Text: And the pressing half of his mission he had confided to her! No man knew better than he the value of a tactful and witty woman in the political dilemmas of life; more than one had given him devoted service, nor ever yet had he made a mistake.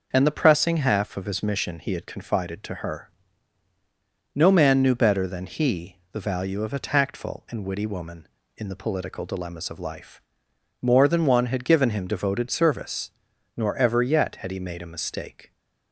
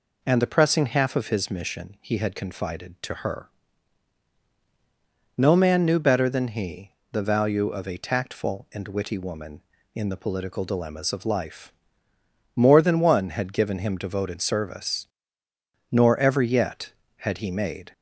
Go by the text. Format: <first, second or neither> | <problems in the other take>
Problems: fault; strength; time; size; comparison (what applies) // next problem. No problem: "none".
first | pauses between "he" and "the"; slight; at 6.9 s; 0.20 s long // stops before "a mistake"; at 17.9 s